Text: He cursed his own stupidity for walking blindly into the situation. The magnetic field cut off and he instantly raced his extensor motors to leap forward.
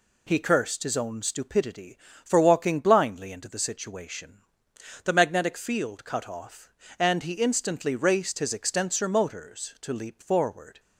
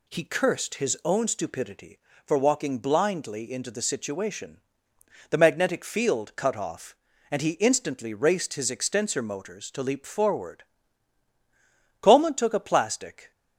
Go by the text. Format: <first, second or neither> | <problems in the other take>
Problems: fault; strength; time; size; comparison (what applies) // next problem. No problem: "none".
first | goes on to say "Coleman took a plastic"; noticeable; from 12.0 s on; 1.3 s long